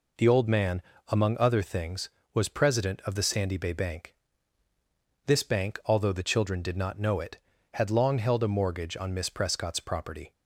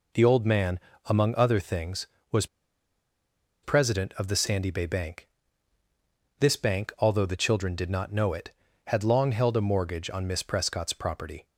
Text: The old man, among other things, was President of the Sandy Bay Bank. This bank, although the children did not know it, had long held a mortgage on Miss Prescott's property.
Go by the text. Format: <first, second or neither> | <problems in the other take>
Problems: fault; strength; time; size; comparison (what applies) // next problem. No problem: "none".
first | pauses between "was" and "President"; at 2.4 s; 1.1 s long